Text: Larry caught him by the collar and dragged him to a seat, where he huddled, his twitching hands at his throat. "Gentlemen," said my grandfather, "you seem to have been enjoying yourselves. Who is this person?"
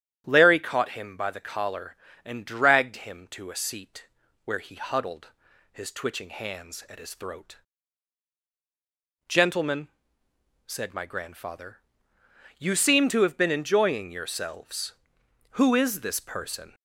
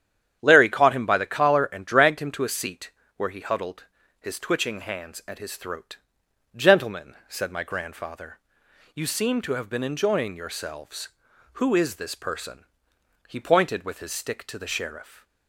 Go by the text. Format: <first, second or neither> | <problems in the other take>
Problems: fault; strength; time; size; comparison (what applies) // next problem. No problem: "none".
first | starts louder than the rest; strong; until 1.4 s; 9.5 dB; strong in the first // goes on to say "He pointed with his stick to the sheriff"; strong; from 13.2 s on; 1.9 s long